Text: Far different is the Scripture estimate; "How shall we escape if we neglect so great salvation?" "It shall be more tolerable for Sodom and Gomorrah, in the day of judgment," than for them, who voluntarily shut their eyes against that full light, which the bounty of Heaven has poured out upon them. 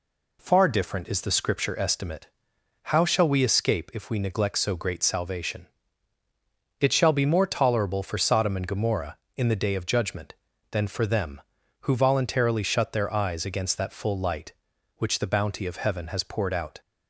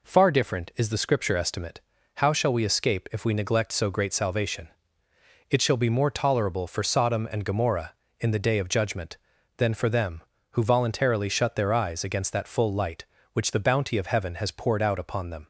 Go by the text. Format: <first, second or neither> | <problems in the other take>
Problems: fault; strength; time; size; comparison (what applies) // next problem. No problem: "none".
second | stops before "upon them"; at 16.8 s